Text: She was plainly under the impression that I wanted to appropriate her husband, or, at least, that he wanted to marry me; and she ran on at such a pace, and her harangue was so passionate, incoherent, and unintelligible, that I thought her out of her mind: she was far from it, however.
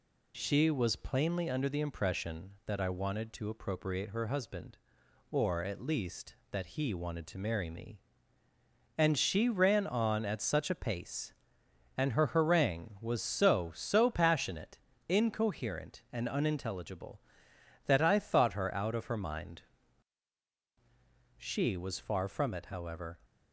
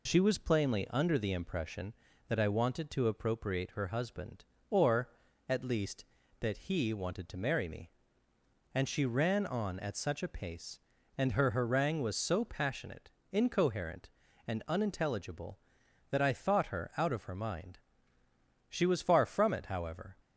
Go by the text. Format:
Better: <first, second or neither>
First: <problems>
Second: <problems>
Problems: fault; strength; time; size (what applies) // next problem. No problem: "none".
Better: second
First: says "so" twice; at 13.7 s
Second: none